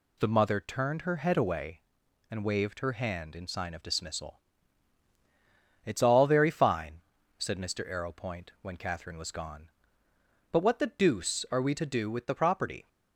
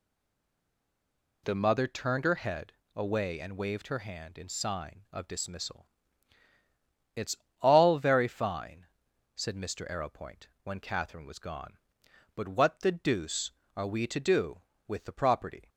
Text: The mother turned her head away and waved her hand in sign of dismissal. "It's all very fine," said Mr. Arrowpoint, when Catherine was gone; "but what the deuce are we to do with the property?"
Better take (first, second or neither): first